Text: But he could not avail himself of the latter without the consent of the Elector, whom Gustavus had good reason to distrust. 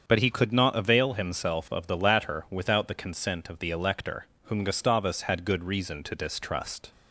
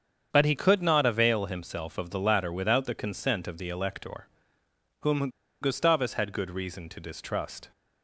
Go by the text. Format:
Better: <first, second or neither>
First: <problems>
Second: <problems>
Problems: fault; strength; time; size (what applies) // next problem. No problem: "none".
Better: first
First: starts louder than the rest; strong; until 1.0 s; 7 dB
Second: starts louder than the rest; strong; until 1.3 s; 7.5 dB // pauses between "whom" and "Gustavus"; slight; at 5.2 s; 0.32 s long